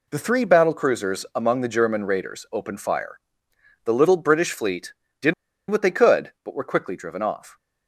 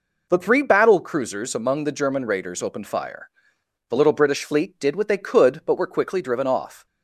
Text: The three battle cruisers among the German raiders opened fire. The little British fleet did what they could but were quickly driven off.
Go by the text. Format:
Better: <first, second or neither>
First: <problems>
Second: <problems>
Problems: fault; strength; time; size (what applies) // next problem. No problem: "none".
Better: second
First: pauses between "did" and "what"; at 5.3 s; 0.36 s long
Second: none